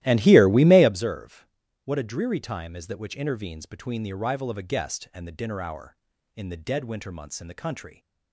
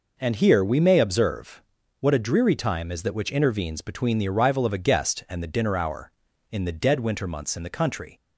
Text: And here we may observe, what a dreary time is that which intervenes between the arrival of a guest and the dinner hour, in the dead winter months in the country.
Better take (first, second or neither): second